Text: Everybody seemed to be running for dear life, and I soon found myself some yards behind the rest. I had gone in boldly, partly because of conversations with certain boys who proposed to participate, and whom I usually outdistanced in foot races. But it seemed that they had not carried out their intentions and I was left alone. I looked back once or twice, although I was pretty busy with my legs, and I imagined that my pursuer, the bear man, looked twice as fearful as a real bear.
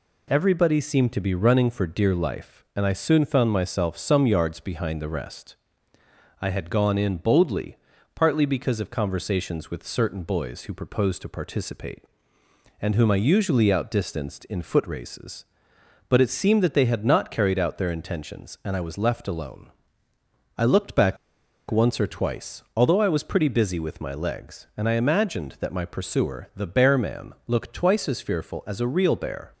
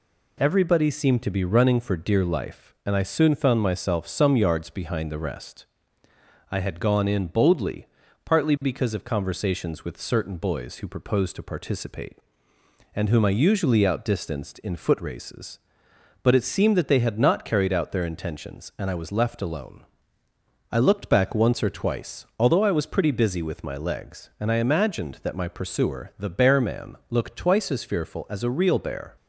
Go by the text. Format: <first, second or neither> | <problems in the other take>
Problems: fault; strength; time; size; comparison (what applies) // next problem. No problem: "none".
second | pauses between "back" and "once"; noticeable; at 21.1 s; 0.53 s long